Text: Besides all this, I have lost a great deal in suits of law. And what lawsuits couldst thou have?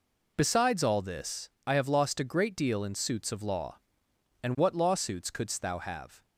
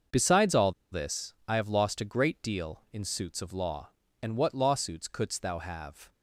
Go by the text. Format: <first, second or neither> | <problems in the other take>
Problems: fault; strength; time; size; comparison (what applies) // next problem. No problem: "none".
first | starts louder than the rest; until 1.3 s; 6 dB // pauses between "all" and "this"; slight; at 0.7 s; 0.18 s long